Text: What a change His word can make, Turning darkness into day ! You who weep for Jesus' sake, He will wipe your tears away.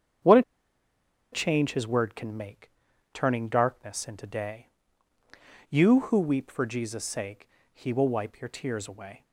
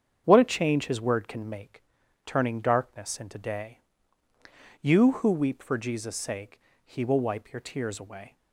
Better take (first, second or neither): second